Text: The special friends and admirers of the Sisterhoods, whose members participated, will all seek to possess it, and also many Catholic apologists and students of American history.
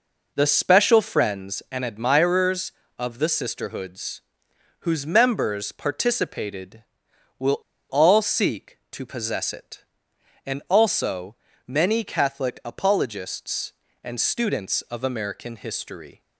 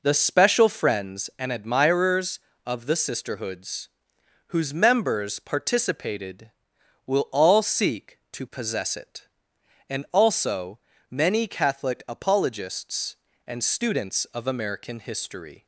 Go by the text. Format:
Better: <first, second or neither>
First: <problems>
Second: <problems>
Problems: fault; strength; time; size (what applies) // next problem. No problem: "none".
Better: second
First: pauses between "will" and "all"; slight; at 7.6 s; 0.28 s long // pauses between "also" and "many"; slight; at 11.3 s; 0.30 s long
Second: pauses between "also" and "many"; slight; at 10.7 s; 0.30 s long